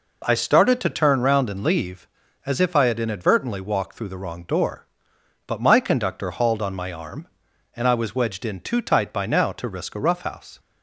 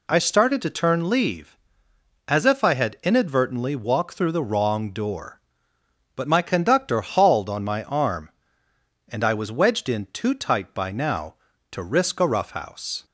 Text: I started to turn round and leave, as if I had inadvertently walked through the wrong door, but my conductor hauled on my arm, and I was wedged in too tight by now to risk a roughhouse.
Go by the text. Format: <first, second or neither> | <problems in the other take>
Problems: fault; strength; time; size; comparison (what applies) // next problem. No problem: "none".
first | skips "round and"; at 1.0 s